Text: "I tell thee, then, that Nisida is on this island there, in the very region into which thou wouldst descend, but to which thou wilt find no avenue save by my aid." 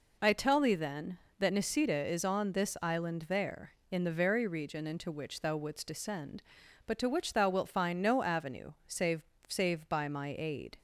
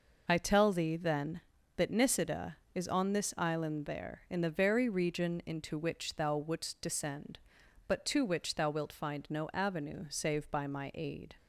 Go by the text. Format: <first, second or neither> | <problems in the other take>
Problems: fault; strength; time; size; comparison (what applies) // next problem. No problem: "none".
second | pauses between "avenue" and "save"; slight; at 8.7 s; 0.16 s long // says "save" twice; at 9.4 s